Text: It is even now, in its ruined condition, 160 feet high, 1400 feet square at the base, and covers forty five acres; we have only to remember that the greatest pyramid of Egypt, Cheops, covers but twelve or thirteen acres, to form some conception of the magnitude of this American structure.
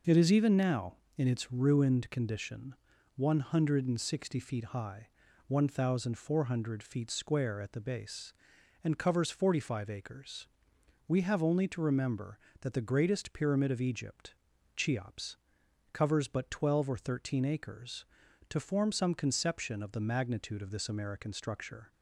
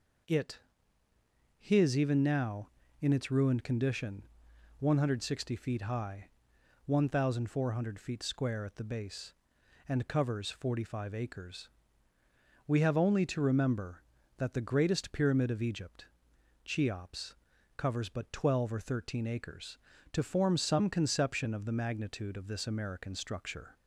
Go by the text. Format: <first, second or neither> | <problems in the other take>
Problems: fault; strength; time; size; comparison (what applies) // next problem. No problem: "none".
first | says "his" for "is"; at 1.5 s